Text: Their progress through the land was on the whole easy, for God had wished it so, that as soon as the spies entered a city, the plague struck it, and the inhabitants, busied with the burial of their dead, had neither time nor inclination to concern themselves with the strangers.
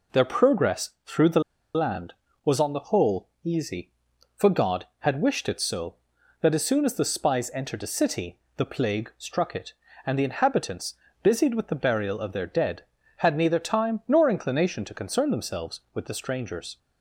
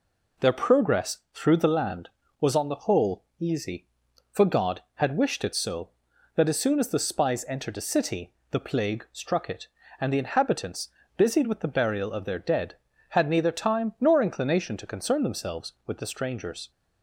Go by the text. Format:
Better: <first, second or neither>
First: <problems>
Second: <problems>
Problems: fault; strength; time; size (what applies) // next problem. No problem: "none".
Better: second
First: pauses between "progress" and "through"; slight; at 0.8 s; 0.16 s long // pauses between "the" and "land"; slight; at 1.3 s; 0.35 s long // pauses between "whole" and "easy"; slight; at 3.2 s; 0.16 s long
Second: pauses between "progress" and "through"; slight; at 1.1 s; 0.16 s long // pauses between "whole" and "easy"; slight; at 3.2 s; 0.16 s long